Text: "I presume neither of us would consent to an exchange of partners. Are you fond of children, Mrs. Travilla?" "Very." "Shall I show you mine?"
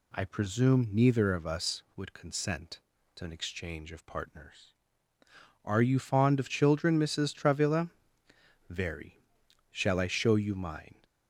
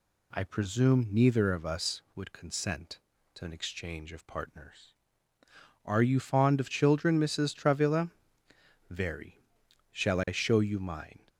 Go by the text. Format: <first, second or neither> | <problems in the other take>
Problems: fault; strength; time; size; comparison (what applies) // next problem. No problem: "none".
neither | none